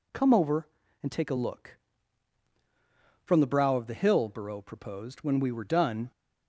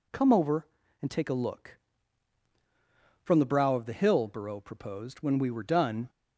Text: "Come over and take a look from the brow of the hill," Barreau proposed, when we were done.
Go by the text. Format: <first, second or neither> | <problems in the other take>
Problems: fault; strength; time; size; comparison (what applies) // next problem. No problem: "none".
neither | none